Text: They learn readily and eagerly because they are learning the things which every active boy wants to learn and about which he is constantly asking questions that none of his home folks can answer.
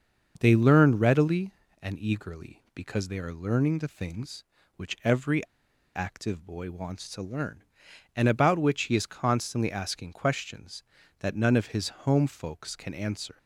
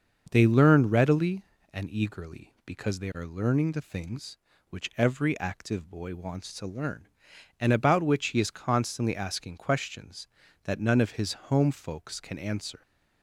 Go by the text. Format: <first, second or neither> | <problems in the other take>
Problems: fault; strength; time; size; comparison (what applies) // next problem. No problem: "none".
second | starts louder than the rest; until 1.4 s; 6.5 dB; also in the second // pauses between "every" and "active"; noticeable; at 5.4 s; 0.51 s long